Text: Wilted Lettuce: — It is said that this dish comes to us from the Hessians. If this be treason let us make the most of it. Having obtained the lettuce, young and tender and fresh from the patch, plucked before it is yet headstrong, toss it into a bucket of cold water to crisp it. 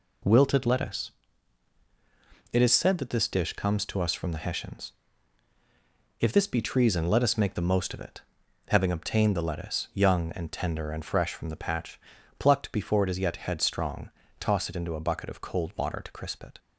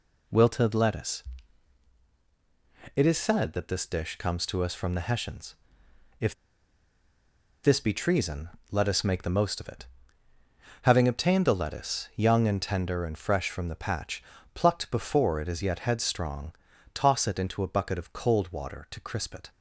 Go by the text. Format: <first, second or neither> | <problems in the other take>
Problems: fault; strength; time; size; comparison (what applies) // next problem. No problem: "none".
first | pauses between "If" and "this"; strong; at 6.3 s; 1.2 s long // pauses between "treason" and "let"; slight; at 8.4 s; 0.22 s long